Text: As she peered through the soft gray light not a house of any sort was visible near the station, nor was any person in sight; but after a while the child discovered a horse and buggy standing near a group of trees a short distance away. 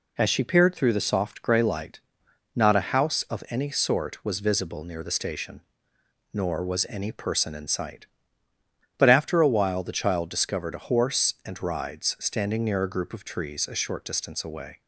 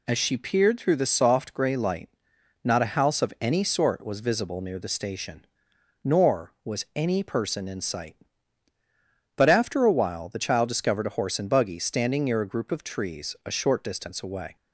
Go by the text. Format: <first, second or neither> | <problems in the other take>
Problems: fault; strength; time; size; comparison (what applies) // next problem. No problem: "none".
second | pauses between "light" and "not"; noticeable; at 1.9 s; 0.56 s long; noticeable in the second // says "rides" for "buggy"; at 11.6 s